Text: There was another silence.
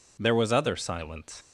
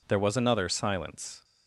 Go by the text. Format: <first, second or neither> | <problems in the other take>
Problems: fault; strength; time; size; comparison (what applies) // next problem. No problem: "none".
second | says "other" for "another"; at 0.5 s